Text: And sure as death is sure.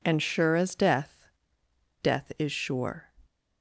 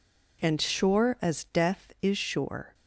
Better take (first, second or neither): second